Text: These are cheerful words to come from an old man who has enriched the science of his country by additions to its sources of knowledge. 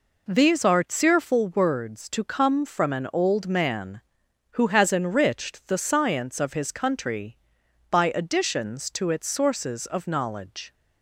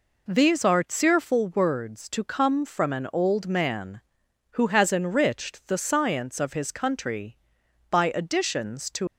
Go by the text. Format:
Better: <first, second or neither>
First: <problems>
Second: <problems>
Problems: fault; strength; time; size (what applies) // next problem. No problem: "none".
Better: first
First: none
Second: stops before "its sources of knowledge"; at 9.0 s